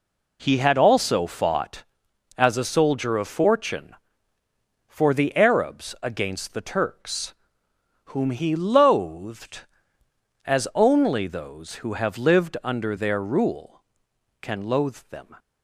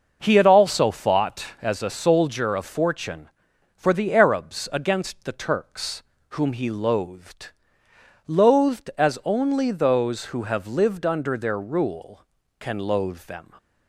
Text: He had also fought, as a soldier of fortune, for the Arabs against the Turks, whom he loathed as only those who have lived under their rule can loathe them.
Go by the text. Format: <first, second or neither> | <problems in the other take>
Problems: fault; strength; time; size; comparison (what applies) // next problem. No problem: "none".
first | says "loathed" twice; at 8.2 s